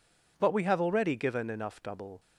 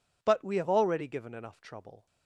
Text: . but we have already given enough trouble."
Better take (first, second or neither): second